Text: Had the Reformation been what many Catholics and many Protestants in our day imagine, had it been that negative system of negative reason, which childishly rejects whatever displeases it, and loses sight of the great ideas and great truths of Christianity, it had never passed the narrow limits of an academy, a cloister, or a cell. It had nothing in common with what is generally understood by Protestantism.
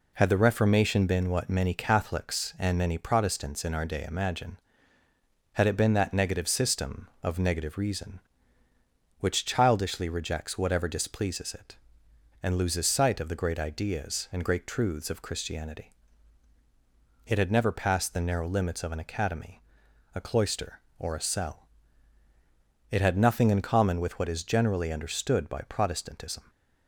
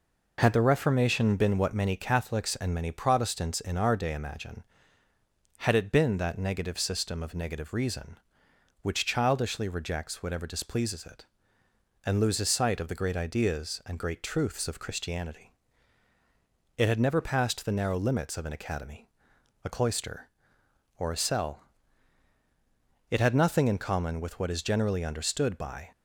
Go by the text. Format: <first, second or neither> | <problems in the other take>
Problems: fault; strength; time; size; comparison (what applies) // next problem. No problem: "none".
first | stops before "Protestantism"; at 25.9 s